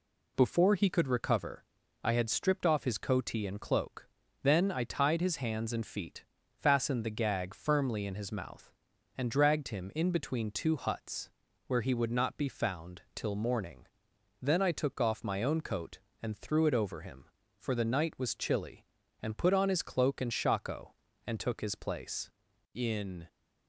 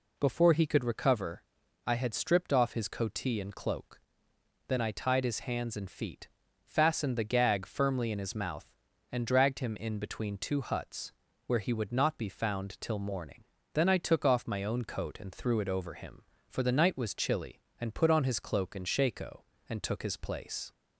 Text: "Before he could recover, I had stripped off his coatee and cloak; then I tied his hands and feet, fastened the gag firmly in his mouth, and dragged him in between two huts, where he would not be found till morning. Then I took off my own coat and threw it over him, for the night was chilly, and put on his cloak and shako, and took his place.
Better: second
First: goes on to say "In"; from 22.7 s on; 0.52 s long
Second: none

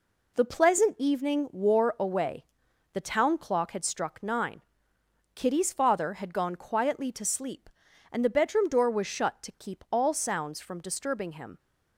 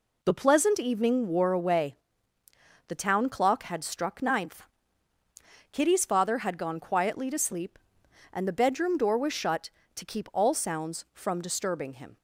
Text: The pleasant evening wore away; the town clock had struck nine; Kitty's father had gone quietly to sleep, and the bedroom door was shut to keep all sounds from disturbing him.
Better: first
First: none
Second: says "ninth" for "nine"; at 4.2 s

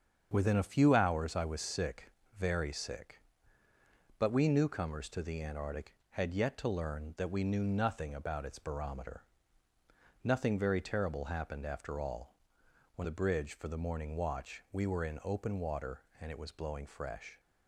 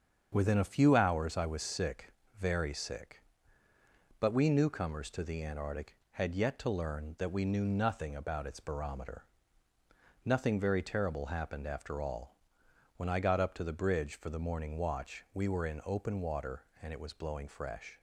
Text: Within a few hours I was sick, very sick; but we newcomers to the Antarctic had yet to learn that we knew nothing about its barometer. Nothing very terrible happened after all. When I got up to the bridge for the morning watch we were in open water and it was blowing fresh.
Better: second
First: starts louder than the rest; until 1.3 s; 7 dB // skips "I got up to"; at 13.0 s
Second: starts louder than the rest; strong; until 1.3 s; 7 dB

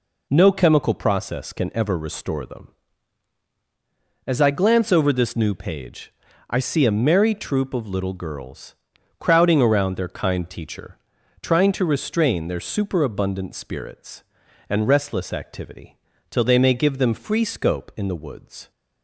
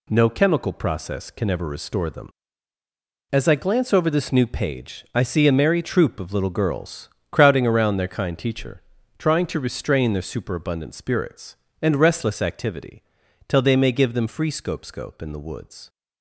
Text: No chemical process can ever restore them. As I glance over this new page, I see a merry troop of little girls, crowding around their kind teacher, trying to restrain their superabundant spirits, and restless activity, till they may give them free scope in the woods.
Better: first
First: none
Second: says "scope" twice; at 14.8 s

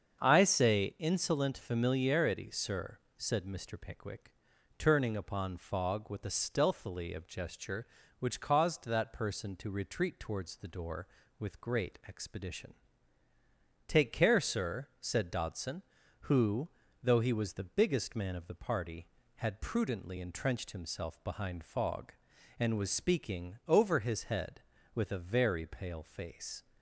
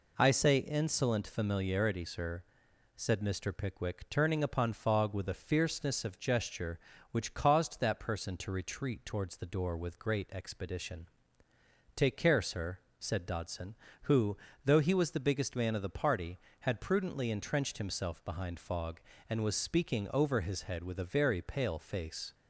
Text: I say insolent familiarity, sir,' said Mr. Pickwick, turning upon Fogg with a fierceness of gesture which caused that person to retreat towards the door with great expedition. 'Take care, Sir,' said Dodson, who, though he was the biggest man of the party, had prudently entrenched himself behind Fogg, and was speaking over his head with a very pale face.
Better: second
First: starts louder than the rest; until 1.2 s; 7 dB // says "stealthily" for "fierceness"; at 6.2 s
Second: none

